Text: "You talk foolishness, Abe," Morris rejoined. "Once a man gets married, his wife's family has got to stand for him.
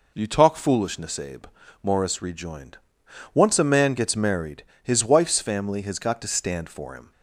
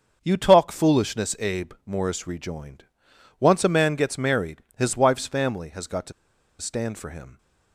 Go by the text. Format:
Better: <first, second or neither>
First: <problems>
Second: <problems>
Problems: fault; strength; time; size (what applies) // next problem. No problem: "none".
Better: first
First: none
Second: starts louder than the rest; until 1.2 s; 7 dB // pauses between "to" and "stand"; noticeable; at 6.1 s; 0.47 s long